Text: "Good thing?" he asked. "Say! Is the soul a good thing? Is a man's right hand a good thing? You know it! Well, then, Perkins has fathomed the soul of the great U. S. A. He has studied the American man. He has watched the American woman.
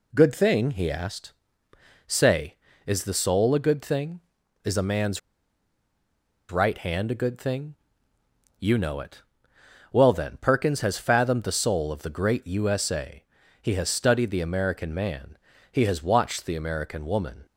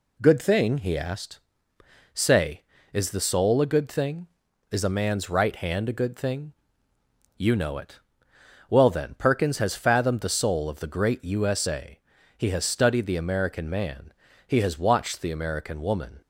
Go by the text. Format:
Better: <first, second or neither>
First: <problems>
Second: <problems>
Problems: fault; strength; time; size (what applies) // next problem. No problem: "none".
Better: second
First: pauses between "man's" and "right"; strong; at 5.1 s; 1.3 s long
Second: none